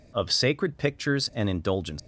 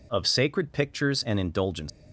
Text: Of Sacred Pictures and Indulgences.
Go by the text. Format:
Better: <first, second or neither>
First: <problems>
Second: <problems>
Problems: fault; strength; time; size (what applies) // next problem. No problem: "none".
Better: neither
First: none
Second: none